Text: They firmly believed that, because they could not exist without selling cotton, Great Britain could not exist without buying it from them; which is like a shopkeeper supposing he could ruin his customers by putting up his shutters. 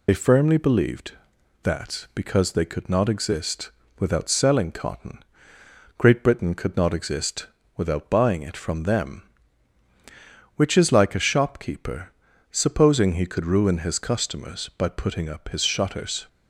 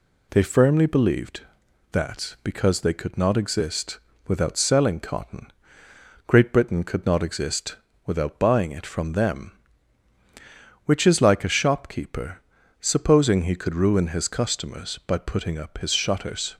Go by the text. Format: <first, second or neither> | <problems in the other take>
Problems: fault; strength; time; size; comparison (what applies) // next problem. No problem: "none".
second | loses the start of "They"; at 0.0 s; 60 ms // pauses between "exist" and "without"; slight; at 3.7 s; 0.28 s long; slight in the second // pauses between "exist" and "without"; slight; at 7.4 s; 0.28 s long; slight in the second // pauses between "shopkeeper" and "supposing"; at 12.1 s; 0.38 s long; also in the second